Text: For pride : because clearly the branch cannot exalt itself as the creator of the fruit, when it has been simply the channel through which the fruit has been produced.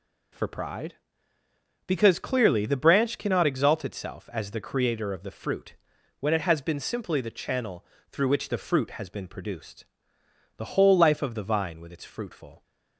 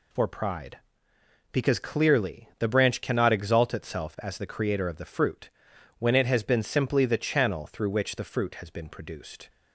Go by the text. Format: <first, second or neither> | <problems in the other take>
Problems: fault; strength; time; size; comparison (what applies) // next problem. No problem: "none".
second | pauses between "channel" and "through"; slight; at 7.8 s; 0.26 s long // goes on to say "The whole life of the vine with its fruitful"; strong; from 10.5 s on; 2.0 s long